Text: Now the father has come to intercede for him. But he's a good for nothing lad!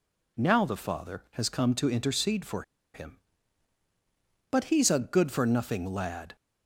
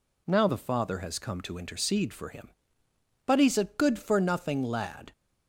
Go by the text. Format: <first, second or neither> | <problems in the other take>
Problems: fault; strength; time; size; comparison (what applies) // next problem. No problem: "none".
second | pauses between "for" and "him"; slight; at 2.6 s; 0.32 s long